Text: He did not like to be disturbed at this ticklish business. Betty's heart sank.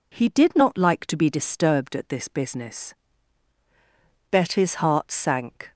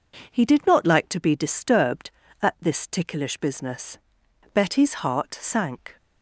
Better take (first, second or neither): second